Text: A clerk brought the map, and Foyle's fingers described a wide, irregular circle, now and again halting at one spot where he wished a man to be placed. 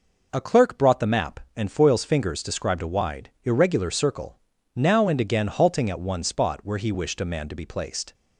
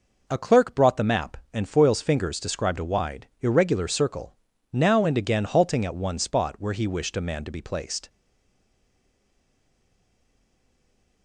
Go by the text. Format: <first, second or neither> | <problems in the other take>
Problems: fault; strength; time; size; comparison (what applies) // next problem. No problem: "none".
first | stays silent after the last word; strong; from 8.0 s on; 3.2 s long